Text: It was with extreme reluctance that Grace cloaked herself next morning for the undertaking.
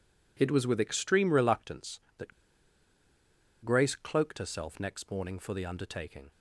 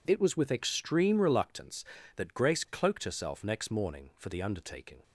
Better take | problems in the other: second | pauses between "that" and "Grace"; strong; at 2.3 s; 1.3 s long

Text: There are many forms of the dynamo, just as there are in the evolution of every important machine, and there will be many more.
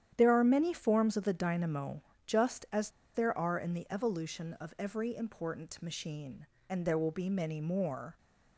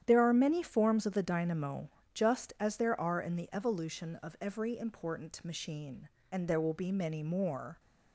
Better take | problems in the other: second | starts louder than the rest; strong; until 1.1 s; 10 dB; strong in the second // pauses between "as" and "there"; slight; at 2.8 s; 0.24 s long

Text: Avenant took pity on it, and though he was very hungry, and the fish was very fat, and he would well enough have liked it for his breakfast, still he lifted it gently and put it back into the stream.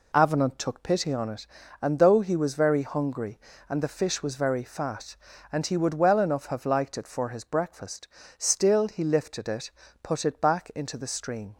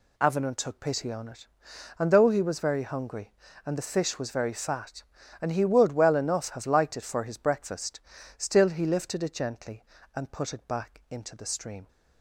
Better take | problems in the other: second | skips "gently and"; at 9.8 s

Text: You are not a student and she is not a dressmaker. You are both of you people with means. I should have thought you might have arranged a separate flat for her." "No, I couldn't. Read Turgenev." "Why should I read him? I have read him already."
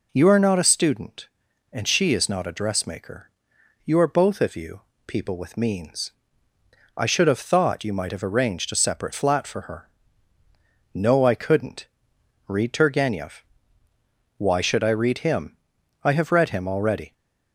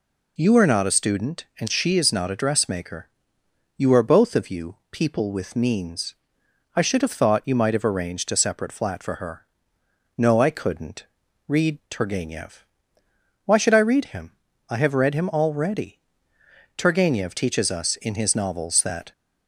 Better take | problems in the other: first | pauses between "you" and "people"; slight; at 4.7 s; 0.16 s long; slight in the first // goes on to say "Turgenev teaches us in his novels that"; strong; from 16.7 s on; 2.3 s long

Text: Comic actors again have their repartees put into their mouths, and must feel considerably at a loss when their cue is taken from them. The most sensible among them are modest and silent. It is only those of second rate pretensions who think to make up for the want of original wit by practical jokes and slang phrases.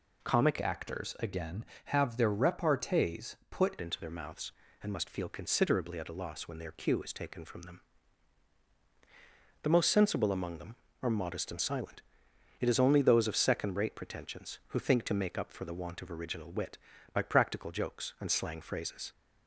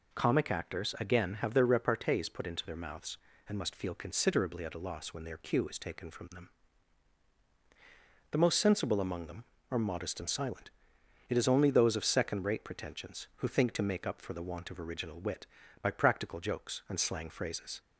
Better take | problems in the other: second | changes voice from "actors" to "put"; from 0.6 to 3.7 s; 3.1 s long

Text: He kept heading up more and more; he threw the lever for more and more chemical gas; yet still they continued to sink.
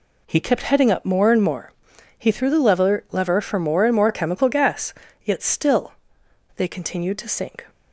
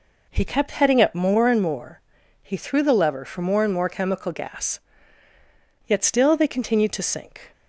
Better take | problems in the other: second | says "lever" twice; at 3.1 s // pauses between "still" and "they"; noticeable; at 5.9 s; 0.62 s long

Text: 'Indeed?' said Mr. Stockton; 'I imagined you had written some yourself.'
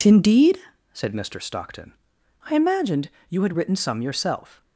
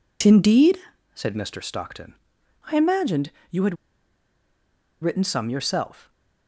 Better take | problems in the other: first | pauses between "imagined" and "you"; slight; at 3.3 s; 0.18 s long; slight in the first // pauses between "had" and "written"; strong; at 3.7 s; 1.2 s long

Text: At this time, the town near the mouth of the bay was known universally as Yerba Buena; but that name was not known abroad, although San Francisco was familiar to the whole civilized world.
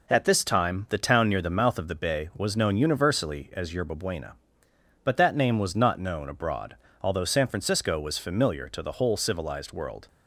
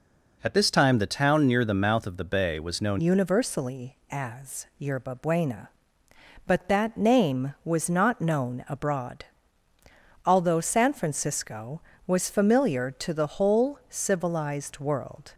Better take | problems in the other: first | changes voice at "universally"; from 2.9 s on; 12.4 s long

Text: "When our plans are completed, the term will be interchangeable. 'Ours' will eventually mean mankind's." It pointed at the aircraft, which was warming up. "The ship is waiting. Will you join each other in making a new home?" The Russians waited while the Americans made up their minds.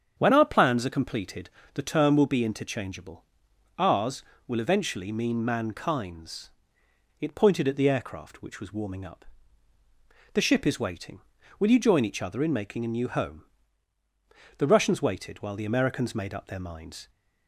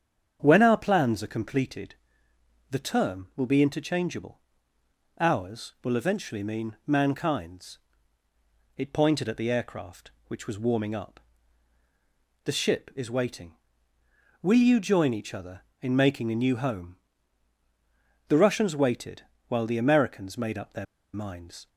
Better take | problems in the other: first | starts louder than the rest; strong; until 1.4 s; 8 dB; strong in the first // pauses between "waited" and "while"; slight; at 19.2 s; 0.24 s long // pauses between "their" and "minds"; slight; at 20.8 s; 0.30 s long

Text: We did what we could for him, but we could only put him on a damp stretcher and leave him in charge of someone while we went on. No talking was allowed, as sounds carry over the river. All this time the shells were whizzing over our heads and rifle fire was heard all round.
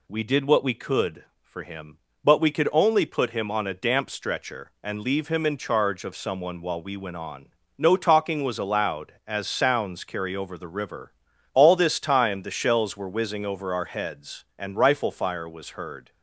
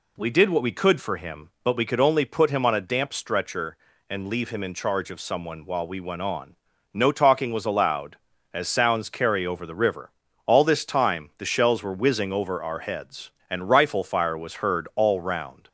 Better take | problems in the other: second | stops before "all round"; at 16.1 s

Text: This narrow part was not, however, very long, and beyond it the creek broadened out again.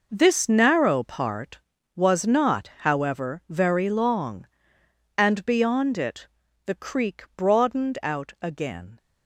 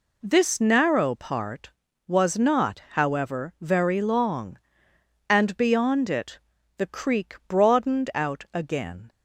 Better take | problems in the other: second | gets quieter; strong; throughout; 10.5 dB // pauses between "it" and "the"; slight; at 6.2 s; 0.36 s long; slight in the second

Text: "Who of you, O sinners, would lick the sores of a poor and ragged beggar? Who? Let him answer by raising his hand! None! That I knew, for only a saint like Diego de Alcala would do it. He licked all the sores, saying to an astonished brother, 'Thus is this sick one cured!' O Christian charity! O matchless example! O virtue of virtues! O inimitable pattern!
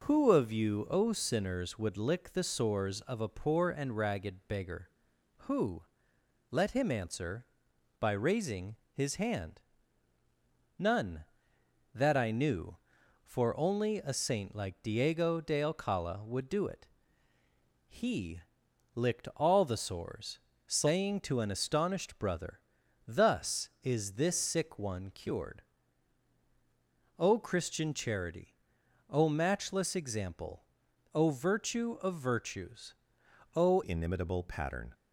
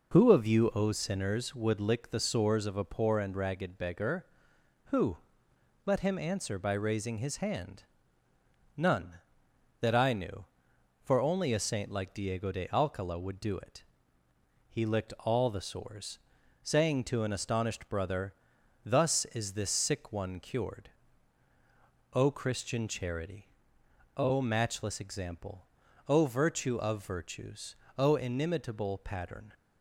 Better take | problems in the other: second | pauses between "raising" and "his"; slight; at 8.7 s; 0.18 s long // pauses between "He" and "licked"; noticeable; at 18.4 s; 0.56 s long // changes voice at "inimitable"; from 33.8 s on; 1.1 s long

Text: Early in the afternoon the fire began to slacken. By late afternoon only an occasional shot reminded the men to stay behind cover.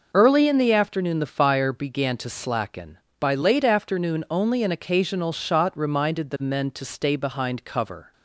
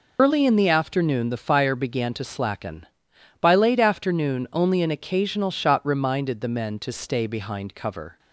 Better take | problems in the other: first | loses the start of "Early"; at 0.1 s; 85 ms

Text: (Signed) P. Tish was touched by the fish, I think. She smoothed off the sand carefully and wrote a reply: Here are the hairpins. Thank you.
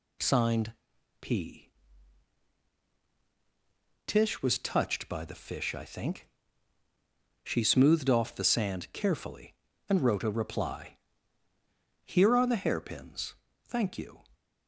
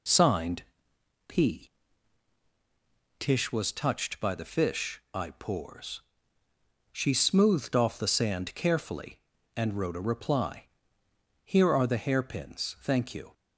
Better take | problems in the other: first | says "pours" for "think"; at 5.3 s

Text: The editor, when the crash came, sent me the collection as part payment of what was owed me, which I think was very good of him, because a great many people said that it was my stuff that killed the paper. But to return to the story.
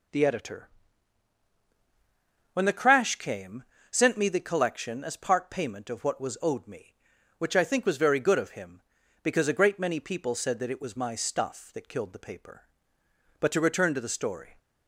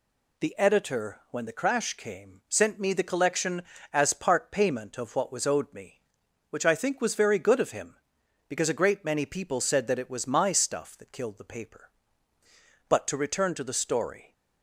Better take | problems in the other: neither | none

